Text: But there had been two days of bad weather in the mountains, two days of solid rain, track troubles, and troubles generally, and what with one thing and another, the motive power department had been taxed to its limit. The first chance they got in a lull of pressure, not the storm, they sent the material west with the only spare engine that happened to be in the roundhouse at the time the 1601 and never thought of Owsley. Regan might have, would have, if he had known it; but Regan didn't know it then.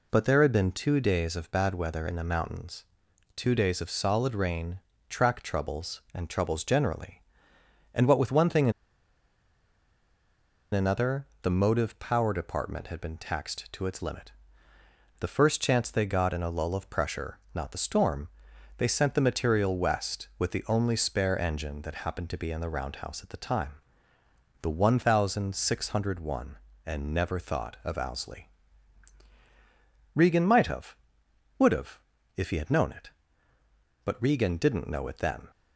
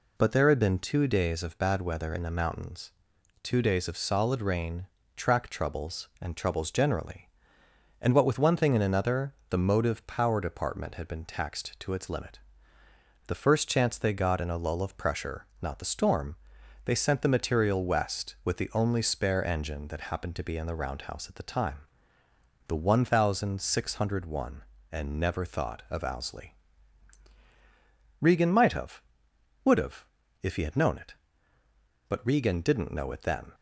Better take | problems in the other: second | pauses between "and" and "another"; strong; at 8.7 s; 2.0 s long // pauses between "time" and "the"; noticeable; at 23.7 s; 0.90 s long; noticeable in the second

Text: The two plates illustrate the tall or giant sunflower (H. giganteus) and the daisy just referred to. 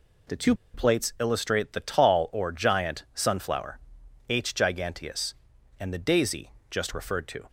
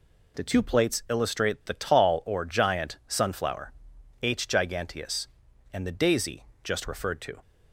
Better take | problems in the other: second | pauses between "two" and "plates"; slight; at 0.5 s; 0.19 s long // pauses between "daisy" and "just"; slight; at 6.5 s; 0.18 s long; slight in the second

